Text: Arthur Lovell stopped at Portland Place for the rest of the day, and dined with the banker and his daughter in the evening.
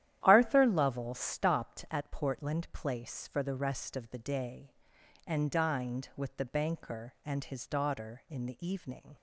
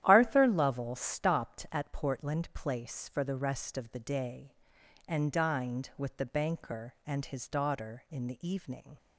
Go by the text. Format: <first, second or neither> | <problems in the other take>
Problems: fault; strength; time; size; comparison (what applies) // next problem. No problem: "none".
neither | starts louder than the rest; strong; the same in both